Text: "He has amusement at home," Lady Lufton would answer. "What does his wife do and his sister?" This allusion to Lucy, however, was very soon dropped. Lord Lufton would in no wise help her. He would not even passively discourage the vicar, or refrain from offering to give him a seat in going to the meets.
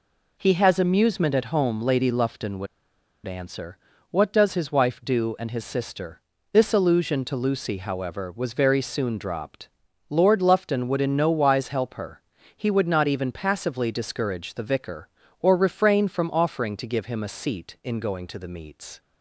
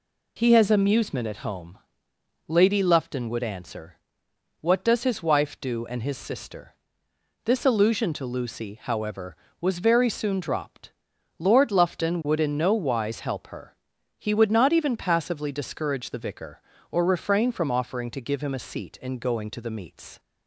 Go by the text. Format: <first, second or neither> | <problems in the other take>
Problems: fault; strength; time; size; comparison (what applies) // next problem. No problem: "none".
second | pauses between "would" and "answer"; noticeable; at 2.6 s; 0.59 s long